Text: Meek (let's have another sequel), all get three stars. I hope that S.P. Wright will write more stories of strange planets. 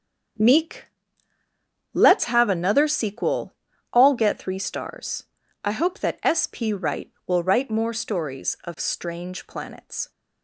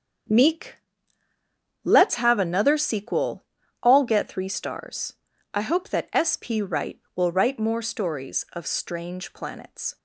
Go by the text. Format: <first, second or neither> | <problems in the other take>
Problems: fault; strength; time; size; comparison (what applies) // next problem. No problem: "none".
neither | starts louder than the rest; strong; the same in both